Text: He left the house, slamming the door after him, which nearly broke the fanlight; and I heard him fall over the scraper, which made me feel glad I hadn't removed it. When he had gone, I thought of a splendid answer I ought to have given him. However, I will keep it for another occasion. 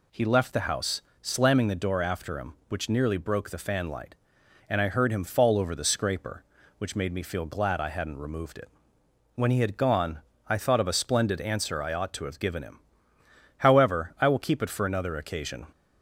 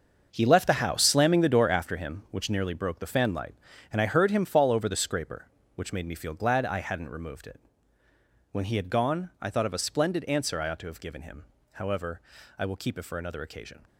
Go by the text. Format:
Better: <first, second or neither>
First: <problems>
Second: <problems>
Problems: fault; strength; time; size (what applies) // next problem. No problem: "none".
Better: first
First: none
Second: gets quieter; strong; throughout; 12 dB